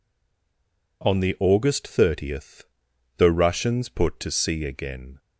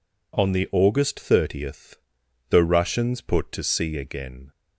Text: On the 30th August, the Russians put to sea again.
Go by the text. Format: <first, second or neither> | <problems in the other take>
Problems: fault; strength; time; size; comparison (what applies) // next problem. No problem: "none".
second | stays silent before the first word; until 1.0 s; 1.0 s long